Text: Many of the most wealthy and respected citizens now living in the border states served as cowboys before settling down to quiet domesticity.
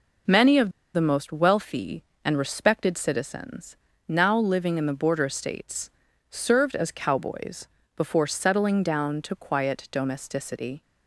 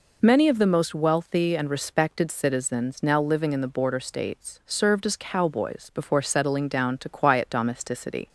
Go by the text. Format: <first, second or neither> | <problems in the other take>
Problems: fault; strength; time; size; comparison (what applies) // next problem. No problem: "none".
second | pauses between "of" and "the"; slight; at 0.7 s; 0.24 s long // pauses between "citizens" and "now"; slight; at 3.7 s; 0.32 s long // pauses between "states" and "served"; at 5.9 s; 0.40 s long // pauses between "cowboys" and "before"; slight; at 7.6 s; 0.28 s long